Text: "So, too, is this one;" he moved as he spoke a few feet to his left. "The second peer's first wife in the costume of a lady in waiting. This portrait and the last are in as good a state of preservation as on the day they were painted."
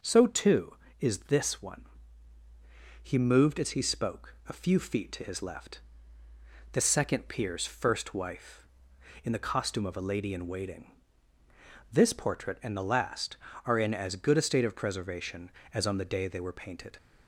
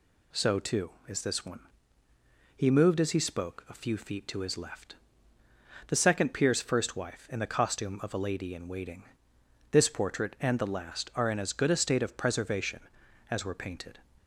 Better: first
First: none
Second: skips "on the day they"; at 13.4 s

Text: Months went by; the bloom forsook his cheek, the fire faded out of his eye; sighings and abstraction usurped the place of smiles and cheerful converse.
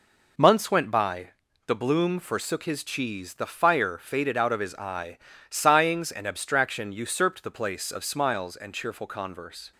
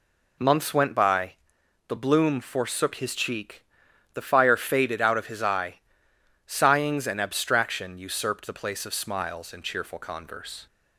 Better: second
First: says "cheese" for "cheek"; at 2.8 s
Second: none

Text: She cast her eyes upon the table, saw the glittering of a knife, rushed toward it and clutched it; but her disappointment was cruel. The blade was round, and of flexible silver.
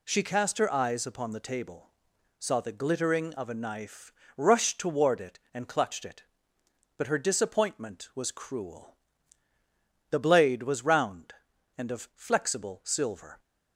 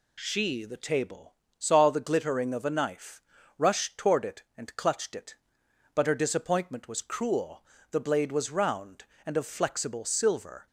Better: first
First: none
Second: skips "cast her eyes upon"; at 0.6 s

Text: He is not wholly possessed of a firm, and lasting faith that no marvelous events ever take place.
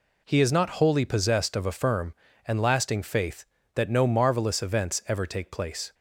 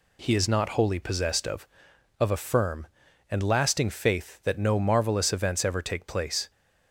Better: first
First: none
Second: says "of" twice; at 2.2 s

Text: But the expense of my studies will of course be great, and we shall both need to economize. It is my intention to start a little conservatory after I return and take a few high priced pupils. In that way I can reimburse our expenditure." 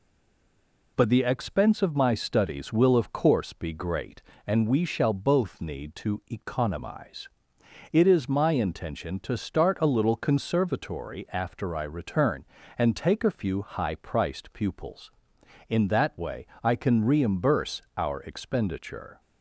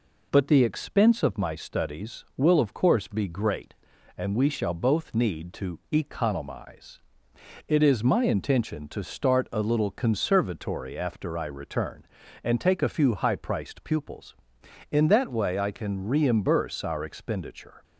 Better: second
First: stays silent before the first word; slight; until 0.9 s; 0.9 s long // pauses between "way" and "I"; slight; at 16.4 s; 0.16 s long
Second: none

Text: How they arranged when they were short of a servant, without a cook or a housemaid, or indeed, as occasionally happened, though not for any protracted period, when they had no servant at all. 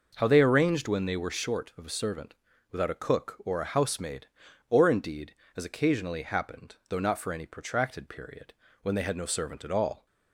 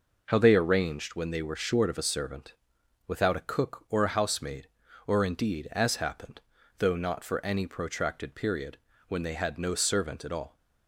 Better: first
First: none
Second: skips "occasionally"; at 5.9 s

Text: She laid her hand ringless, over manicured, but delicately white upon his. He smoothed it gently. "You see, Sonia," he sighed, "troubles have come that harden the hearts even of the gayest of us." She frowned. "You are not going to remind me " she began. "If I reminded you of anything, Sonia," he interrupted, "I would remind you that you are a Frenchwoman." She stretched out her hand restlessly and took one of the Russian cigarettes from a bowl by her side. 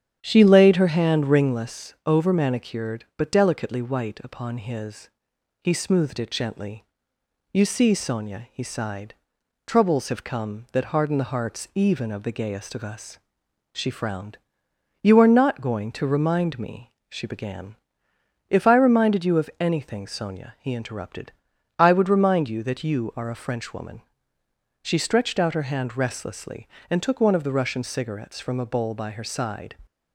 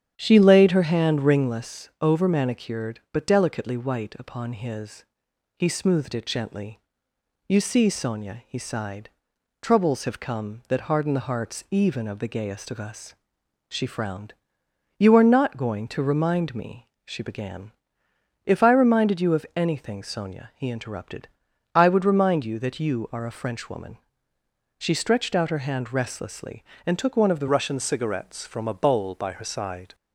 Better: first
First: starts louder than the rest; strong; until 1.2 s; 9 dB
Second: starts louder than the rest; strong; until 1.1 s; 9.5 dB // changes voice at "Russian"; from 27.4 s on; 2.5 s long

